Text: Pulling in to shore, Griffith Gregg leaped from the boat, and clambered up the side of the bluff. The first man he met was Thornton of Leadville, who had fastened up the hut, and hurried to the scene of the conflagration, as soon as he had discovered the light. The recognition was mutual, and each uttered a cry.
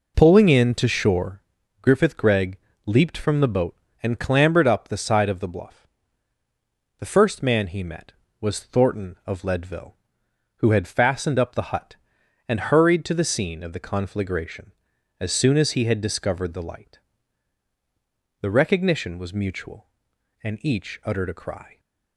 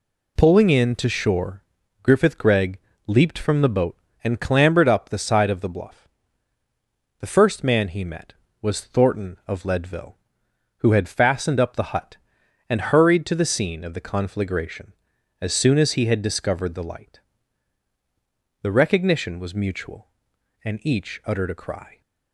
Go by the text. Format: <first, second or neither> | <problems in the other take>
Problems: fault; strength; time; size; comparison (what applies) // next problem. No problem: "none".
second | starts louder than the rest; noticeable; until 1.4 s; 4.5 dB // pauses between "Gregg" and "leaped"; slight; at 2.5 s; 0.28 s long; slight in the second